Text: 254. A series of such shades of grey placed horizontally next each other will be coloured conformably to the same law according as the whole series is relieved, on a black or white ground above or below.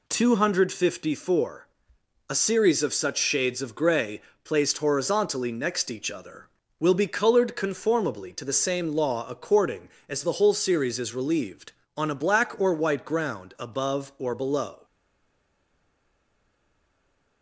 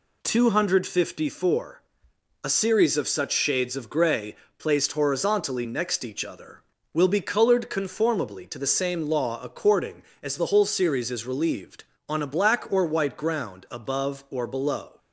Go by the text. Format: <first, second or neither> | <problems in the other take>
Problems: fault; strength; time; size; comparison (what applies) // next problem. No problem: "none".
second | pauses between "grey" and "placed"; slight; at 4.2 s; 0.22 s long; slight in the second // stays silent after the last word; strong; from 14.8 s on; 2.6 s long